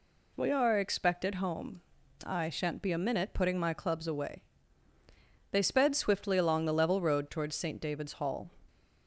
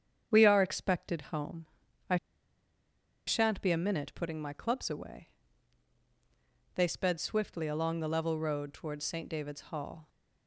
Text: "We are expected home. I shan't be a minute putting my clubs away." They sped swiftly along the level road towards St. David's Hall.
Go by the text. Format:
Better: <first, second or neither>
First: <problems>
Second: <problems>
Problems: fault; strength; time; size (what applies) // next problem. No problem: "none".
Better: first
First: none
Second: starts louder than the rest; strong; until 1.4 s; 8 dB // pauses between "I" and "shan't"; at 2.1 s; 1.1 s long